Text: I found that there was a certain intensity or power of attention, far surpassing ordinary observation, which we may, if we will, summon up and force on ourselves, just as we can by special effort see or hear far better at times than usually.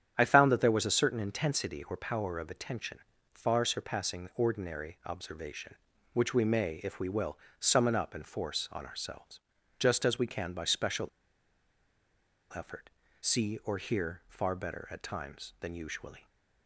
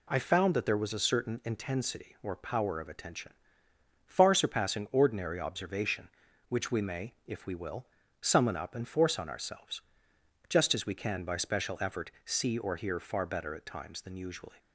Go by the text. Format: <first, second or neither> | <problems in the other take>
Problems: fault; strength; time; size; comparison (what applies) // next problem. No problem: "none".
second | starts louder than the rest; strong; until 1.1 s; 9 dB // pauses between "special" and "effort"; strong; at 11.0 s; 1.4 s long // pauses between "effort" and "see"; slight; at 12.8 s; 0.36 s long